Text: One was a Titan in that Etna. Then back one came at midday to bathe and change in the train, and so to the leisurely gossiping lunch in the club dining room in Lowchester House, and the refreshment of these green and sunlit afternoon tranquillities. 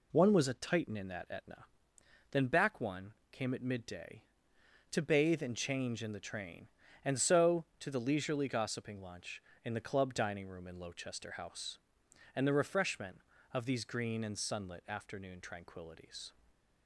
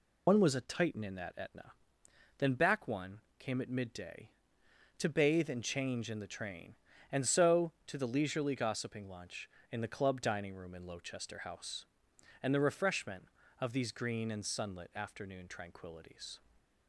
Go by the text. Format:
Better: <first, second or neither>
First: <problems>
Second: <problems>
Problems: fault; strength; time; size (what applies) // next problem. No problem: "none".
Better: first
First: pauses between "one" and "came"; slight; at 3.1 s; 0.18 s long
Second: loses the start of "One"; at 0.2 s; 80 ms // pauses between "one" and "came"; slight; at 3.1 s; 0.18 s long